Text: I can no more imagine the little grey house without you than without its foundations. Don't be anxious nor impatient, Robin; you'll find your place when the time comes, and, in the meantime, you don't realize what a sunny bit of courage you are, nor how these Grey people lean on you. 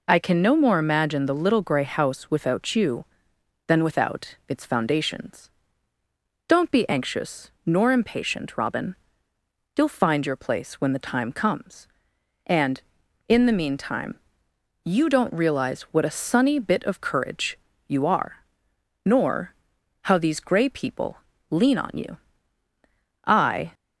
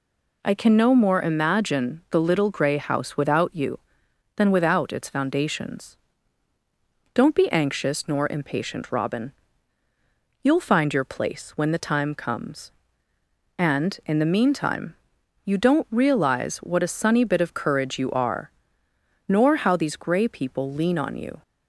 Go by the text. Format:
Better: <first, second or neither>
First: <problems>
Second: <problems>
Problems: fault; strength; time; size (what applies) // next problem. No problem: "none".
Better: second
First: pauses between "courage" and "you"; slight; at 17.5 s; 0.30 s long // pauses between "nor" and "how"; noticeable; at 19.5 s; 0.50 s long // pauses between "people" and "lean"; at 21.1 s; 0.40 s long // goes on to say "I"; slight; from 23.2 s on; 0.48 s long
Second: none